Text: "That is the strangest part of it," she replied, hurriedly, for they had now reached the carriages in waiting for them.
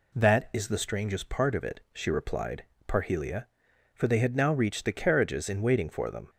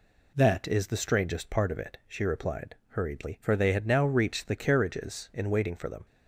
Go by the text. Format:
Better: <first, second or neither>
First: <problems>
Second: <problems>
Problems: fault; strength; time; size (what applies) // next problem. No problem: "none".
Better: second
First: says "parhelia" for "hurriedly"; at 2.8 s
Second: none